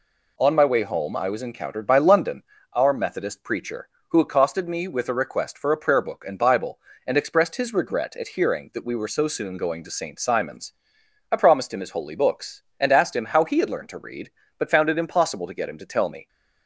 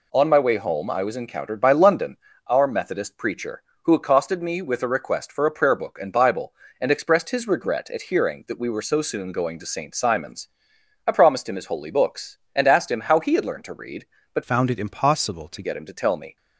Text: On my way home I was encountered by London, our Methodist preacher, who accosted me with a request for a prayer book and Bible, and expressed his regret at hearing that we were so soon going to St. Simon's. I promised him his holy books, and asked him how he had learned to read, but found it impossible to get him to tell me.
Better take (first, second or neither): first